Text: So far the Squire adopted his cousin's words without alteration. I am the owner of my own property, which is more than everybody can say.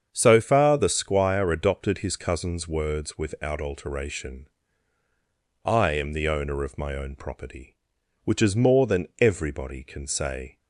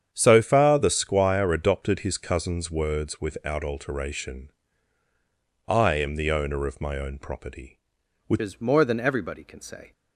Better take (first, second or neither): first